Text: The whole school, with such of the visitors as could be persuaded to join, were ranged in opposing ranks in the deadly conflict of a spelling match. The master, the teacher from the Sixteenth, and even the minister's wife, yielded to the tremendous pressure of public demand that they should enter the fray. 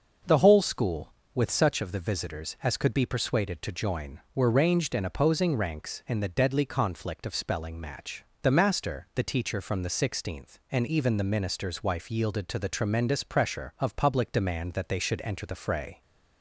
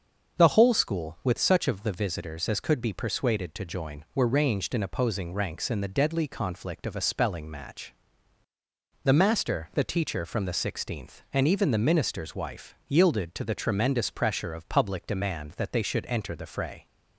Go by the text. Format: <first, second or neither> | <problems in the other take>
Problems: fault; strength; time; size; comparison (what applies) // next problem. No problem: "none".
second | starts louder than the rest; noticeable; until 1.4 s; 6 dB; also in the second // skips "a"; at 7.3 s